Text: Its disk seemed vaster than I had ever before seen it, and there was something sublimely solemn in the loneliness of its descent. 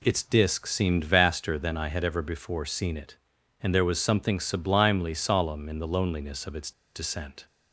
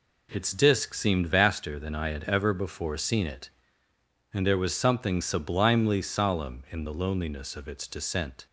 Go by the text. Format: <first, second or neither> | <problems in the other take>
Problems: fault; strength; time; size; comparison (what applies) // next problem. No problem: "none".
second | pauses between "its" and "descent"; slight; at 6.7 s; 0.23 s long